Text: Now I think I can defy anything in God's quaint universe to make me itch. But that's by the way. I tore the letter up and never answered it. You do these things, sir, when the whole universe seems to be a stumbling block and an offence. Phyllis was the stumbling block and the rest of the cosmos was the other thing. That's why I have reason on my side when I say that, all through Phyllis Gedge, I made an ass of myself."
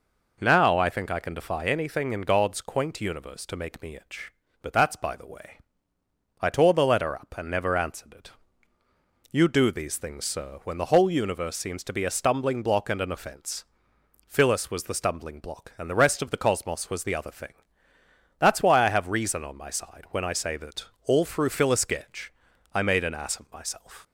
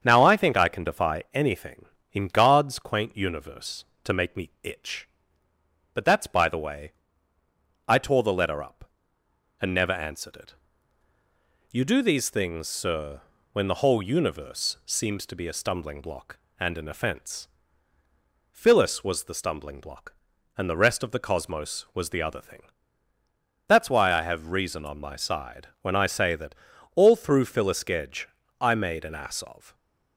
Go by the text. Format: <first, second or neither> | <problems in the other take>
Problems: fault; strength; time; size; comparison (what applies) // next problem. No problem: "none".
first | starts louder than the rest; strong; until 1.0 s; 7.5 dB // stops before "myself"; at 29.7 s